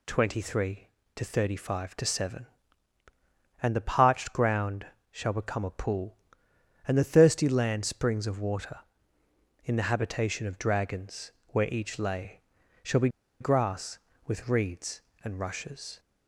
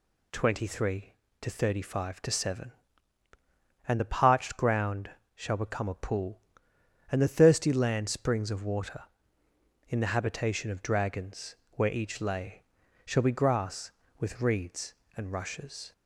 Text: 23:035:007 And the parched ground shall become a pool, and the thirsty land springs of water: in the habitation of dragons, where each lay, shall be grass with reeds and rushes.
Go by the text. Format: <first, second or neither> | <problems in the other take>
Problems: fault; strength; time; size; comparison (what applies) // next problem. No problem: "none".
second | pauses between "ground" and "shall"; slight; at 4.8 s; 0.24 s long; slight in the second // pauses between "be" and "grass"; slight; at 13.0 s; 0.32 s long